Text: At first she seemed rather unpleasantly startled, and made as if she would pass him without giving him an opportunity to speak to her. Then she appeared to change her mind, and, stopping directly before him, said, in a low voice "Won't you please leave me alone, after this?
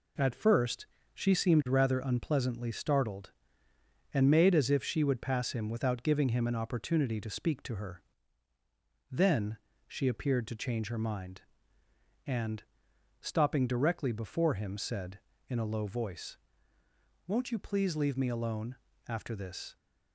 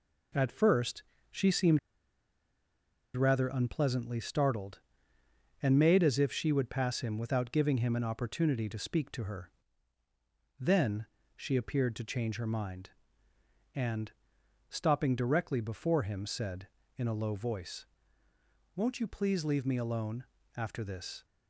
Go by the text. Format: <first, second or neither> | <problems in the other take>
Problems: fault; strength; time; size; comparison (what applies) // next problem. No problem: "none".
first | pauses between "first" and "she"; slight; at 1.0 s; 0.26 s long; slight in the first // pauses between "seemed" and "rather"; strong; at 1.7 s; 1.3 s long // pauses between "Then" and "she"; slight; at 11.0 s; 0.28 s long; slight in the first // pauses between "voice" and "Won't"; noticeable; at 17.8 s; 0.88 s long; noticeable in the first